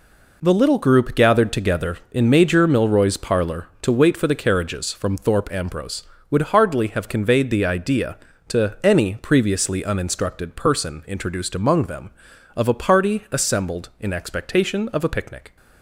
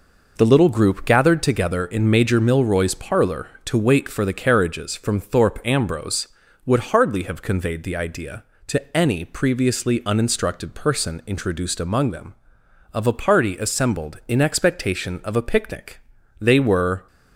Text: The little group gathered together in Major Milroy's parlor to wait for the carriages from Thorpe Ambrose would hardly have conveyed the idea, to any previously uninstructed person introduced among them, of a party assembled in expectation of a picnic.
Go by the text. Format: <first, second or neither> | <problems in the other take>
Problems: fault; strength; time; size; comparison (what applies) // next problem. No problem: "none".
first | goes on to say "They were"; noticeable; from 16.3 s on; 0.68 s long